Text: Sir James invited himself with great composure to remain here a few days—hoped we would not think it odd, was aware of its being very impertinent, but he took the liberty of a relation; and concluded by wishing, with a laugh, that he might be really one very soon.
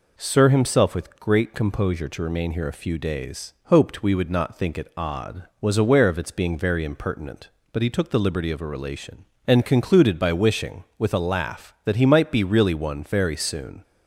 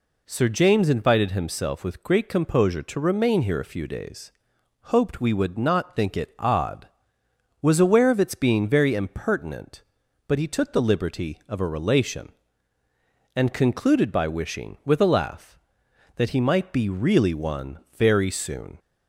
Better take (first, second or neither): second